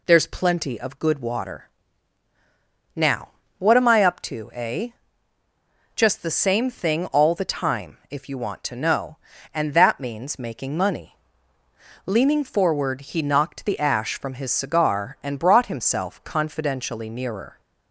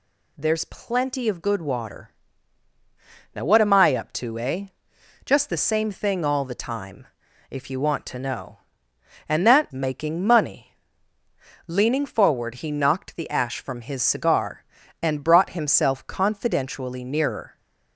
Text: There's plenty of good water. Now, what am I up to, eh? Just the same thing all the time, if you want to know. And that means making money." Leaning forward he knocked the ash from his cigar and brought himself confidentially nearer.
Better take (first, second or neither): first